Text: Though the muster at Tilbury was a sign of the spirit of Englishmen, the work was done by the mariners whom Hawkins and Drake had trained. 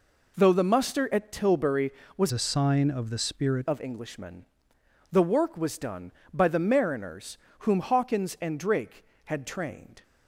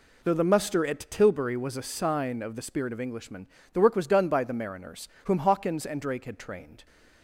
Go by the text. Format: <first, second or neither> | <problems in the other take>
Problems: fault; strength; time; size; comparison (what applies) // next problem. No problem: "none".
second | changes voice from "a" to "spirit"; from 2.3 to 3.6 s; 1.3 s long // pauses between "mariners" and "whom"; slight; at 7.3 s; 0.24 s long; slight in the second